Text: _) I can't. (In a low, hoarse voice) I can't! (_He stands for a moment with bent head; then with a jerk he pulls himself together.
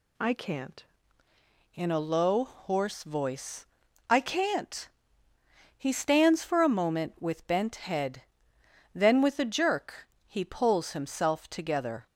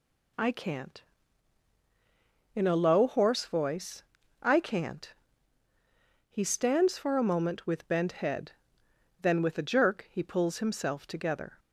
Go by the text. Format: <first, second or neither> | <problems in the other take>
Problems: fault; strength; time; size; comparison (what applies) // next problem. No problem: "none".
second | changes voice at "In"; from 1.7 s on; 10.3 s long // pauses between "jerk" and "he"; slight; at 10.0 s; 0.22 s long